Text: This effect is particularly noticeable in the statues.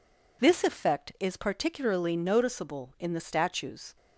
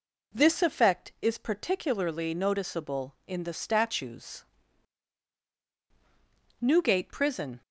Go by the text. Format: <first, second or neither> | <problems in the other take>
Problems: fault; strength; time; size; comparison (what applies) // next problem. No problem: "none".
first | goes on to say "Newgate prison"; noticeable; from 6.5 s on; 1.0 s long